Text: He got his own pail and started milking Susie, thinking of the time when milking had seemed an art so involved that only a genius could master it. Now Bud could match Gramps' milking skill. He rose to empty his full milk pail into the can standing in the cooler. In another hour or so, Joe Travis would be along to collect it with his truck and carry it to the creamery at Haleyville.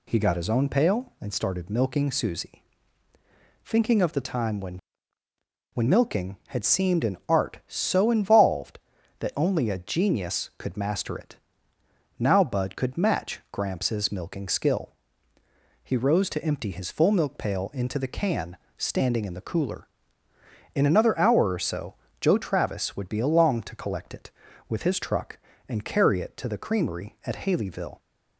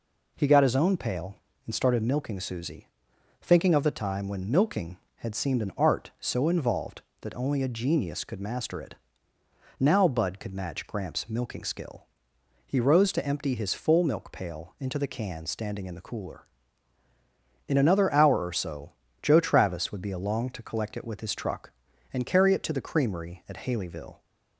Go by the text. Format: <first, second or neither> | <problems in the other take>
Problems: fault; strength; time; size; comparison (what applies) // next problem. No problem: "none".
second | says "when" twice; at 5.7 s // pauses between "can" and "standing"; slight; at 18.5 s; 0.20 s long